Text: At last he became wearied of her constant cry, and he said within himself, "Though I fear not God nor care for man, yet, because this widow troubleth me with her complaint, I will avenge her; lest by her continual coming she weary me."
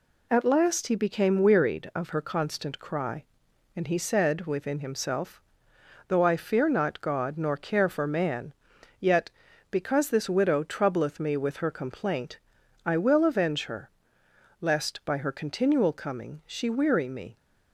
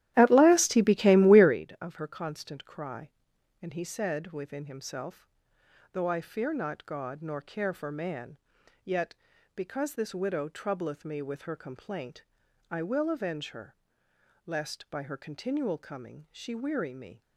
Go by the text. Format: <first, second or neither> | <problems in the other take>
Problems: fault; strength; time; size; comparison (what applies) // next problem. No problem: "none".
first | starts louder than the rest; strong; until 1.6 s; 13.5 dB